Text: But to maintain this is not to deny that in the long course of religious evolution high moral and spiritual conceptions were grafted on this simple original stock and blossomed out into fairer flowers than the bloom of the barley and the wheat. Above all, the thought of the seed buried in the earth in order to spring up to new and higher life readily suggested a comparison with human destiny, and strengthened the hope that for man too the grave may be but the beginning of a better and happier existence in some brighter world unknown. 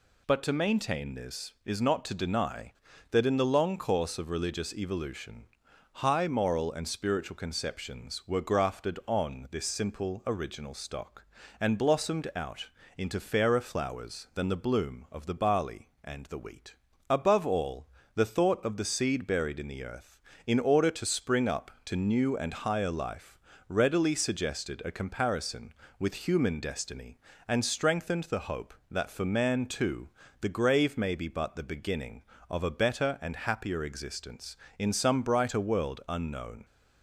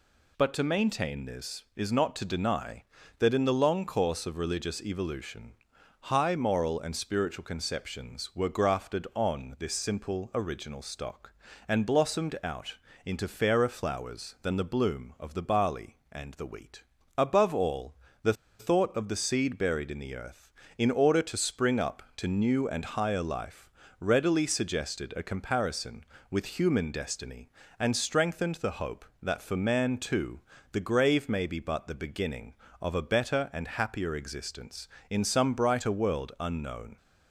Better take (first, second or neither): first